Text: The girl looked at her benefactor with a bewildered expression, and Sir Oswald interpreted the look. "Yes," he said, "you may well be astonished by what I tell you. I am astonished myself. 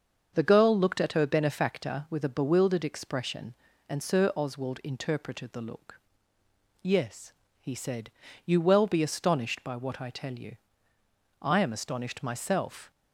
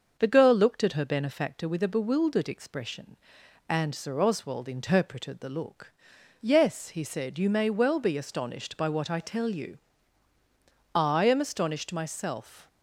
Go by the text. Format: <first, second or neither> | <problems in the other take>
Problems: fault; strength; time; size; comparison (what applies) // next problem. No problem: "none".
second | starts louder than the rest; until 1.3 s; 6.5 dB; also in the second // skips "may"; at 8.6 s